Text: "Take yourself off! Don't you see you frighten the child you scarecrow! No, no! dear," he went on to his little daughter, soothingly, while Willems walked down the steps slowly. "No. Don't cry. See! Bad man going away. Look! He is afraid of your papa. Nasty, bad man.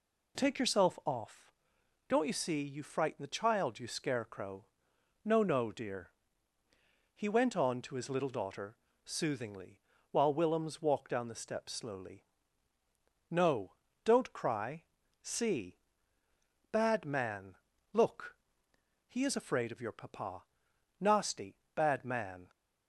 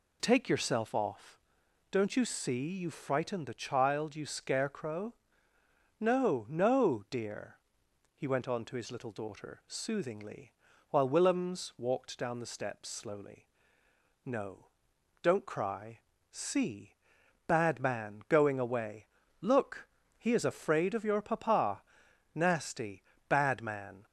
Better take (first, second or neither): second